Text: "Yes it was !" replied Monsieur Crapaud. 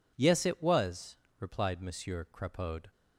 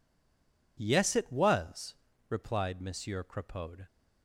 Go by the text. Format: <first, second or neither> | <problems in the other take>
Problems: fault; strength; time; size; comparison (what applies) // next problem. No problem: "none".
first | stays silent before the first word; slight; until 0.7 s; 0.7 s long